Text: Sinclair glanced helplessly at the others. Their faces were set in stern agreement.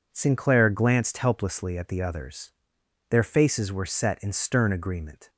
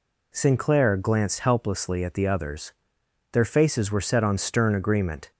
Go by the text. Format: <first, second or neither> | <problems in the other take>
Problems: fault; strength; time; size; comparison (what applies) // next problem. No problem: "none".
first | says "on" for "in"; at 4.2 s